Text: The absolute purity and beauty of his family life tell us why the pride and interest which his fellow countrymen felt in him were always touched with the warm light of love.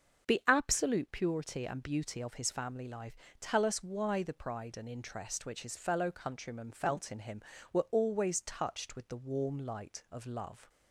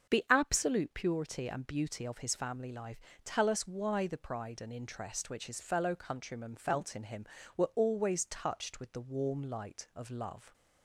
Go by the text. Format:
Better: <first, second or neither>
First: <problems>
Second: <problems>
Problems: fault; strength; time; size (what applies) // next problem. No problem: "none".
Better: neither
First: starts louder than the rest; until 1.3 s; 6.5 dB // pauses between "life" and "tell"; slight; at 3.1 s; 0.24 s long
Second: starts louder than the rest; until 1.1 s; 6.5 dB // pauses between "life" and "tell"; slight; at 3.0 s; 0.24 s long